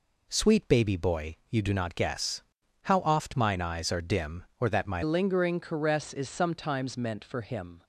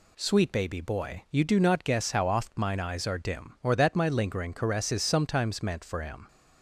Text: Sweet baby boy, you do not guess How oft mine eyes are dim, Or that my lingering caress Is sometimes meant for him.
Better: second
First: pauses between "guess" and "How"; at 2.4 s; 0.40 s long // changes voice at "lingering"; from 5.0 s on; 2.8 s long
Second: none

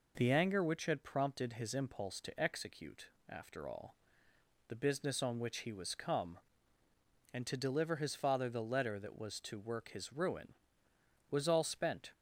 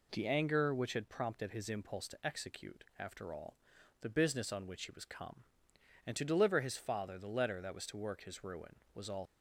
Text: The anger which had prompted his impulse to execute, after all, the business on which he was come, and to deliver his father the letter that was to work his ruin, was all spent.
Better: first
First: none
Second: stops before "spent"; at 9.2 s

